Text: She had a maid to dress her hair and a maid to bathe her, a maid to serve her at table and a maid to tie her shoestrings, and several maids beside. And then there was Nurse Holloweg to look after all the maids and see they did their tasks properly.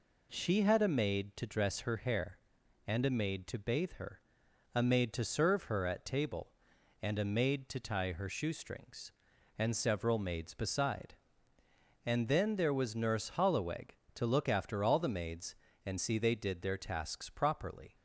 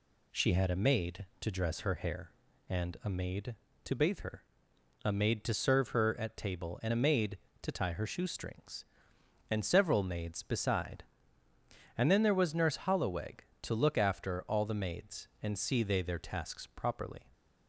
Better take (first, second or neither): first